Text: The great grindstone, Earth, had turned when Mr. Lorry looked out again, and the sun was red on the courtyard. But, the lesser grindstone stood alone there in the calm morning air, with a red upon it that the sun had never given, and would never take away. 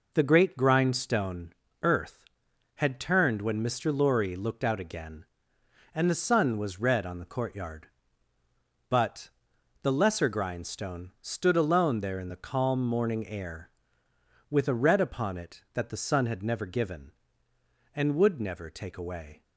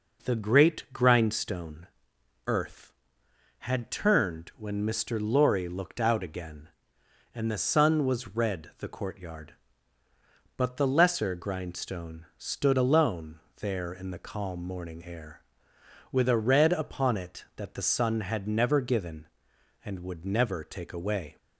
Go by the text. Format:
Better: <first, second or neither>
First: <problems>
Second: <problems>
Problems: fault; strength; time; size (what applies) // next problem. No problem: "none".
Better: first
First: none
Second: skips "on"; at 8.7 s // pauses between "alone" and "there"; slight; at 13.3 s; 0.22 s long